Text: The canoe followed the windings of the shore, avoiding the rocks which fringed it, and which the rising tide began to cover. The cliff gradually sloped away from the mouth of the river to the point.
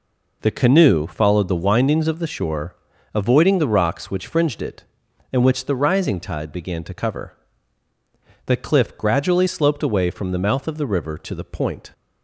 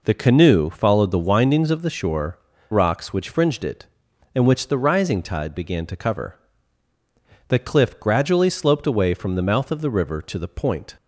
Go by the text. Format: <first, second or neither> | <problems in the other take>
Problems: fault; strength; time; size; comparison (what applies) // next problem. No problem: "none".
first | skips "avoiding the"; at 2.5 s